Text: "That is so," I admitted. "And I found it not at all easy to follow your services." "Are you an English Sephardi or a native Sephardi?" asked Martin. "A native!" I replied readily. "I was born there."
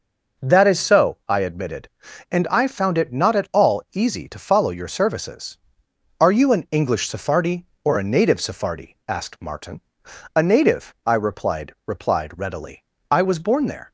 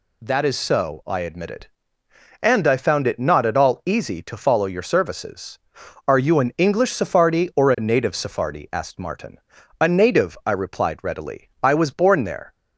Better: second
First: says "replied" twice; at 11.8 s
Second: none

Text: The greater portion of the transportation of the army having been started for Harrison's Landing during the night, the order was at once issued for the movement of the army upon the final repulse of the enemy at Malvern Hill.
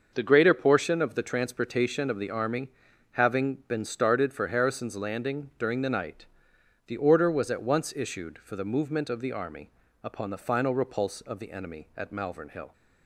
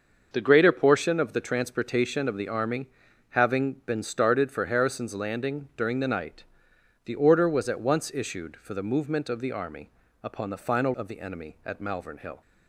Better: first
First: starts louder than the rest; until 1.1 s; 6.5 dB // pauses between "army" and "having"; at 2.6 s; 0.44 s long // pauses between "army" and "upon"; slight; at 9.7 s; 0.32 s long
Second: starts louder than the rest; until 1.3 s; 6.5 dB // pauses between "army" and "having"; at 2.8 s; 0.44 s long // pauses between "army" and "upon"; slight; at 9.9 s; 0.32 s long // skips "repulse"; at 10.9 s

